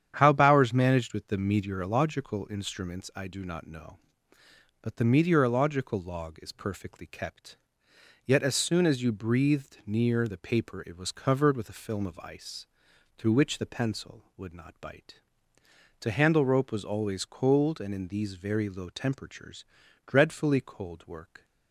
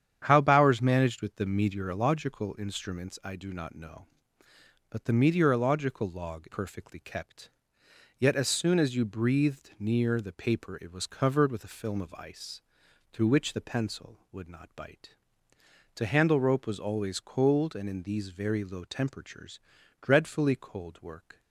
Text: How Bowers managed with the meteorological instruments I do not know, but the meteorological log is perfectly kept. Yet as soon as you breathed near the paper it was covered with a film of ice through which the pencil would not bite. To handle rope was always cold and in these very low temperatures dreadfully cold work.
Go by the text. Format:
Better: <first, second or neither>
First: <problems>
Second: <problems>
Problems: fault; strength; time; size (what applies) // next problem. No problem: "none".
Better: first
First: starts louder than the rest; strong; until 1.1 s; 9 dB // pauses between "ice" and "through"; noticeable; at 12.6 s; 0.50 s long // pauses between "temperatures" and "dreadfully"; at 19.6 s; 0.40 s long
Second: starts louder than the rest; strong; until 1.2 s; 9 dB // skips "is"; at 6.4 s // pauses between "ice" and "through"; noticeable; at 12.6 s; 0.50 s long // pauses between "temperatures" and "dreadfully"; at 19.5 s; 0.40 s long